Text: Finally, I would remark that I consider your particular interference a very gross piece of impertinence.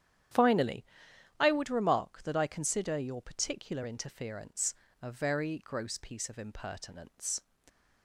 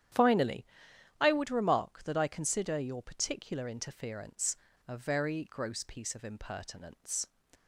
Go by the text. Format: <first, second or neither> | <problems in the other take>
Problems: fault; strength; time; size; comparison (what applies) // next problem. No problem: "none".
neither | starts louder than the rest; strong; the same in both // pauses between "interference" and "a"; slight; the same in both